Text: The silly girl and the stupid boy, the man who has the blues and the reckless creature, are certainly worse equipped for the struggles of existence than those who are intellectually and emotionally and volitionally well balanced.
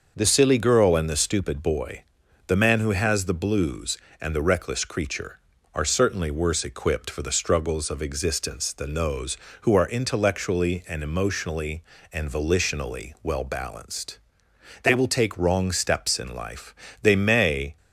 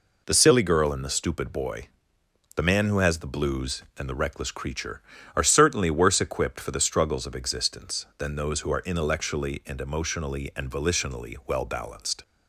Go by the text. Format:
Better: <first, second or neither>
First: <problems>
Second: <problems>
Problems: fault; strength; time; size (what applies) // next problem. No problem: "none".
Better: second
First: starts louder than the rest; until 1.1 s; 6 dB // goes on to say "They will take wrong steps in life they may"; strong; from 14.8 s on; 2.9 s long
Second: none